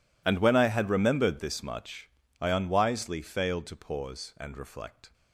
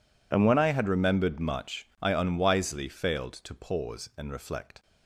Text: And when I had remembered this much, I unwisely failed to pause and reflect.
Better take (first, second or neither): first